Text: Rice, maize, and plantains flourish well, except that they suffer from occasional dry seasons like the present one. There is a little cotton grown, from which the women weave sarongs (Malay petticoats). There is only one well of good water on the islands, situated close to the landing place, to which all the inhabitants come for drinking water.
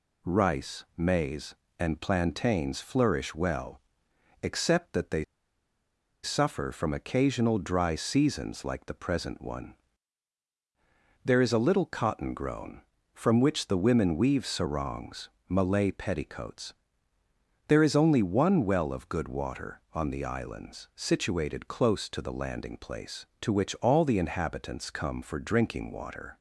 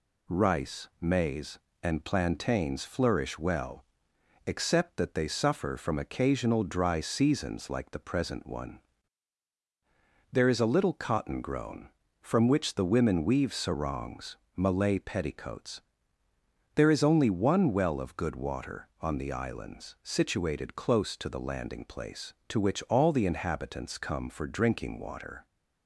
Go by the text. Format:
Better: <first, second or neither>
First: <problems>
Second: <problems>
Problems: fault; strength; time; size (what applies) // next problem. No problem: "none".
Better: second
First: pauses between "they" and "suffer"; at 5.2 s; 0.98 s long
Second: none